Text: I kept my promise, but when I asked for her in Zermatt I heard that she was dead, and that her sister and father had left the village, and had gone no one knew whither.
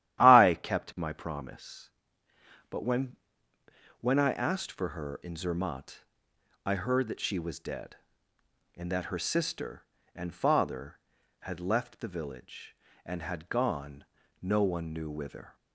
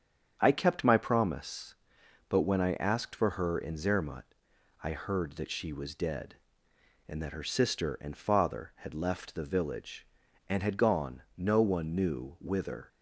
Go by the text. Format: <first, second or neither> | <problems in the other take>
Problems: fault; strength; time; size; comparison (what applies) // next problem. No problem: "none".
second | starts louder than the rest; strong; until 1.3 s; 12 dB; strong in the second // says "when" twice; at 3.9 s // pauses between "Zermatt" and "I"; noticeable; at 6.0 s; 0.60 s long; noticeable in the second // pauses between "gone" and "no"; slight; at 14.0 s; 0.36 s long